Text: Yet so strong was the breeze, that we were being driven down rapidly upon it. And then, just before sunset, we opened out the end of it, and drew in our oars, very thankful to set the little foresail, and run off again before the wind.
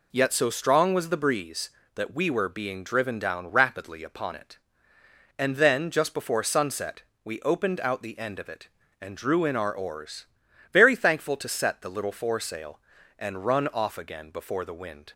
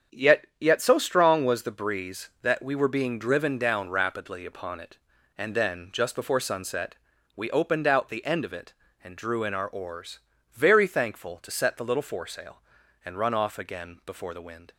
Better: first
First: none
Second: starts louder than the rest; strong; until 1.2 s; 7.5 dB // says "Yet" twice; at 0.5 s

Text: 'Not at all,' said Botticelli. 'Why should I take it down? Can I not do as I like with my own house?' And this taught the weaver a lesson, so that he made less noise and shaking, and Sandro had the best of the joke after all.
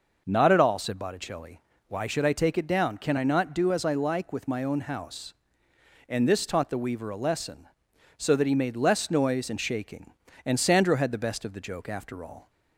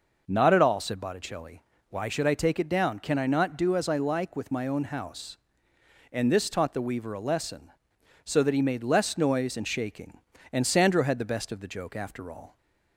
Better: neither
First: none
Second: none

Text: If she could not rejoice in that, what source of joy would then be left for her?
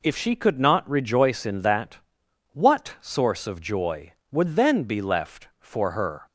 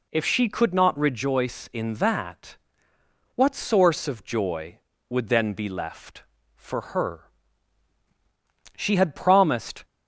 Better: first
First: none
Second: goes on to say "She had promised"; noticeable; from 8.7 s on; 1.0 s long

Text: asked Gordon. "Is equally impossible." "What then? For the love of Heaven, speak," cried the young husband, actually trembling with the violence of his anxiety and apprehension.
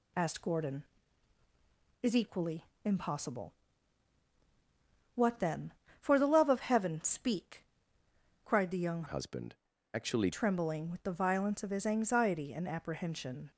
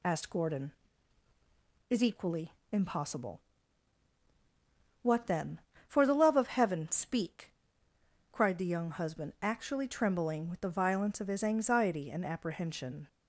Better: second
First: pauses between "equally" and "impossible"; slight; at 2.6 s; 0.18 s long // changes voice from "husband" to "actually"; from 9.0 to 10.2 s; 1.2 s long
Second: pauses between "equally" and "impossible"; slight; at 2.5 s; 0.18 s long

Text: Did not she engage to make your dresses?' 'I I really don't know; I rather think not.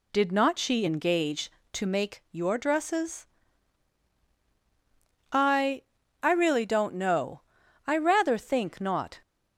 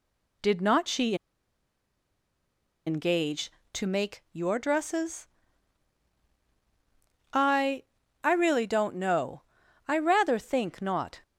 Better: first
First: pauses between "I" and "I"; at 5.8 s; 0.42 s long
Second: pauses between "she" and "engage"; strong; at 1.1 s; 1.7 s long // pauses between "I" and "I"; at 7.8 s; 0.42 s long

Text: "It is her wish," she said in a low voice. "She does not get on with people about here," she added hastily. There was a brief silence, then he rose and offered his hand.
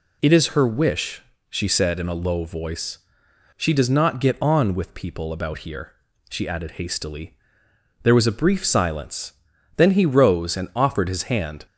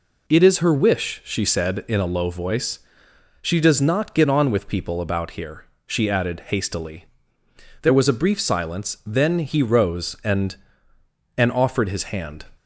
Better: first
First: none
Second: says "and" twice; at 11.3 s

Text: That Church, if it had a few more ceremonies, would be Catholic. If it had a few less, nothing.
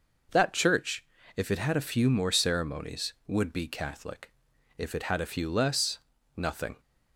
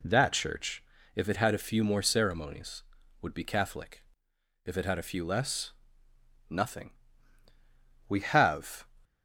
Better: first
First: none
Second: goes on to say "We have"; noticeable; from 8.0 s on; 0.78 s long

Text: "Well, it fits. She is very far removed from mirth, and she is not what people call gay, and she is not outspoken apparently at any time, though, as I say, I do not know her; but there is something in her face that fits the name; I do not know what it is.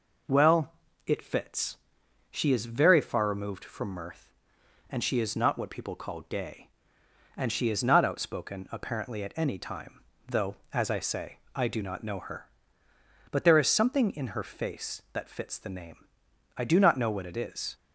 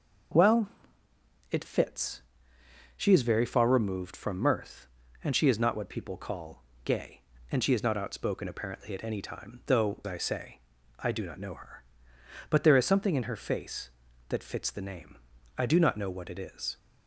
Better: first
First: none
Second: pauses between "call" and "gay"; slight; at 6.6 s; 0.22 s long // skips "as"; at 10.0 s

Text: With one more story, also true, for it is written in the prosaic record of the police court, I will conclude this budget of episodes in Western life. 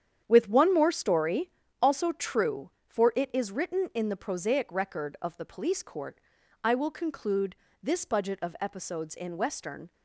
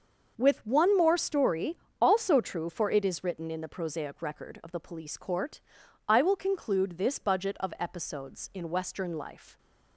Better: second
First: starts louder than the rest; strong; until 1.2 s; 9 dB // pauses between "conclude" and "this"; slight; at 7.5 s; 0.26 s long // stops before "life"; at 9.9 s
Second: starts louder than the rest; until 1.3 s; 6 dB

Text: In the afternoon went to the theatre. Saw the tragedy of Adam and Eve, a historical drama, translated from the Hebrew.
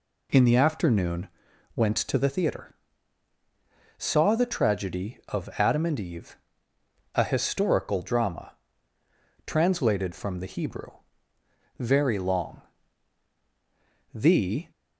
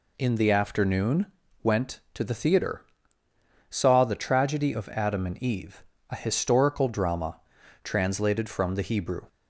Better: second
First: pauses between "afternoon" and "went"; noticeable; at 1.2 s; 0.46 s long // goes on to say "Very long The"; strong; from 11.7 s on; 2.9 s long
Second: pauses between "afternoon" and "went"; slight; at 1.2 s; 0.34 s long

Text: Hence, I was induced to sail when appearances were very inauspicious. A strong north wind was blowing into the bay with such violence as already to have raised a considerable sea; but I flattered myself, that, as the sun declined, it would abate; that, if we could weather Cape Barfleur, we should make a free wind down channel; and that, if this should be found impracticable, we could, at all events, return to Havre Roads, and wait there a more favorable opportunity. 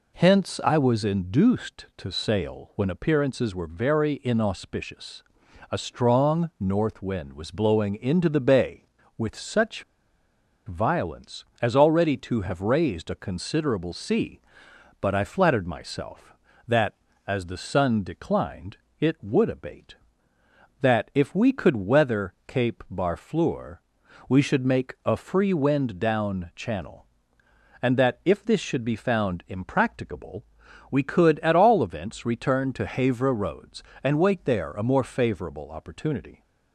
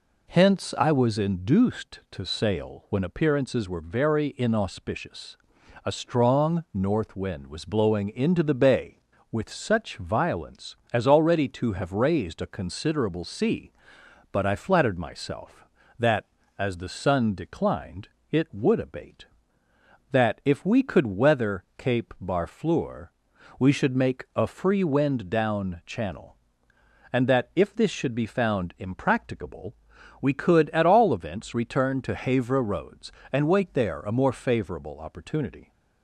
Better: second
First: pauses between "such" and "violence"; noticeable; at 9.8 s; 0.84 s long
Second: none

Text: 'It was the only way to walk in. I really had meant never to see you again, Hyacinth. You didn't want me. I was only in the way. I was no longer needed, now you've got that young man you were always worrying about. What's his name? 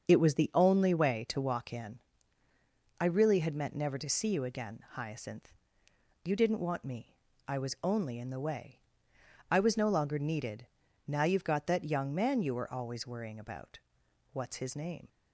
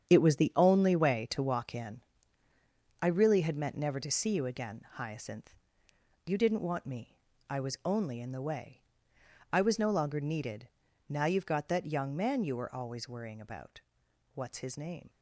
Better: first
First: starts louder than the rest; until 1.1 s; 6.5 dB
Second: gets quieter; strong; throughout; 10 dB // starts louder than the rest; strong; until 1.1 s; 8.5 dB

